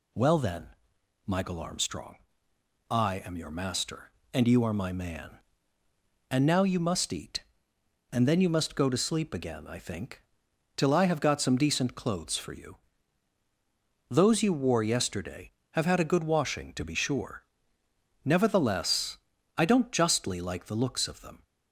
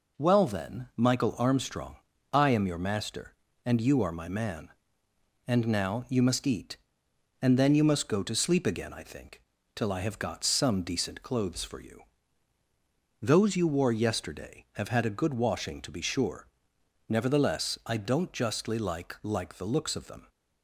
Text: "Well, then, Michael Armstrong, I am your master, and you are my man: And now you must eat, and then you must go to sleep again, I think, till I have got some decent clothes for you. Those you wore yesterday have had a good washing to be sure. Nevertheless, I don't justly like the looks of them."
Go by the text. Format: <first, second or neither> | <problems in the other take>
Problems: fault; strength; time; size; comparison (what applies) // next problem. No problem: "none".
first | says "like" twice; at 19.2 s